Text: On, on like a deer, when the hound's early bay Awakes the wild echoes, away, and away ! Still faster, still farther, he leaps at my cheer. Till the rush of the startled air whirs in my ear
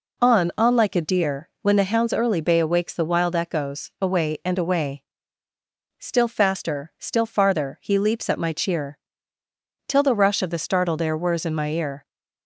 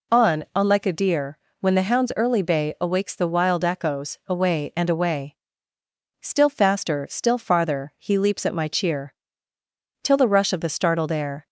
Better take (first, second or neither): first